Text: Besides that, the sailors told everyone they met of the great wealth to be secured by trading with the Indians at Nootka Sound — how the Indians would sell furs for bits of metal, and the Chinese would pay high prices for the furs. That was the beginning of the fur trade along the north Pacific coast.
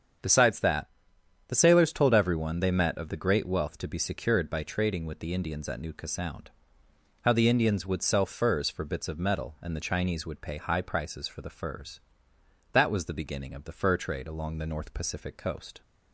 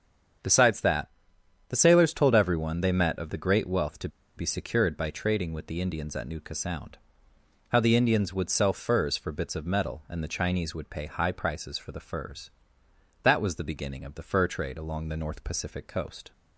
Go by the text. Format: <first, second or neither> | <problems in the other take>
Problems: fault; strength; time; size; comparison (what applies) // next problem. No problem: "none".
first | starts louder than the rest; strong; until 2.0 s; 8 dB; strong in the first // pauses between "to" and "be"; slight; at 4.0 s; 0.29 s long